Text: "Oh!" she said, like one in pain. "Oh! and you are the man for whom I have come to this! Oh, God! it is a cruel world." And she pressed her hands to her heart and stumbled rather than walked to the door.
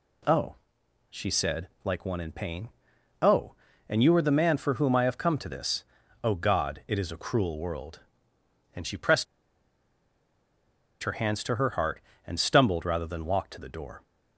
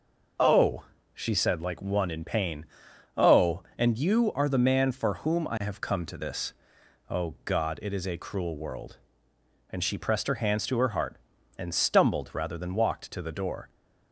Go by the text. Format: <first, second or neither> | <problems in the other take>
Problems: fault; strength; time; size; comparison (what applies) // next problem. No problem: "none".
second | pauses between "pressed" and "her"; strong; at 9.2 s; 1.7 s long